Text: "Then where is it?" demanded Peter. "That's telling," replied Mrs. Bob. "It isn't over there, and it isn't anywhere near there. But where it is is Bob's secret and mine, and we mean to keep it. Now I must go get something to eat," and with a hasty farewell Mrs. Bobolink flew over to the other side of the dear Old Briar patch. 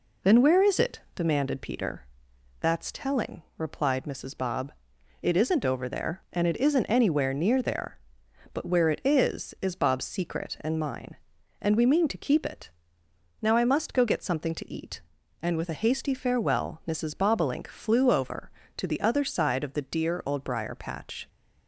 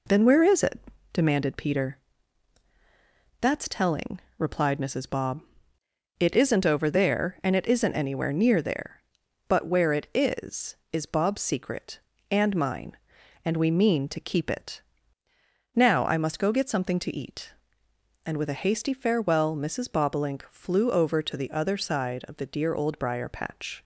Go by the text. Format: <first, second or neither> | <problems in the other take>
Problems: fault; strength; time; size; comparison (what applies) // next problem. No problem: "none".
neither | none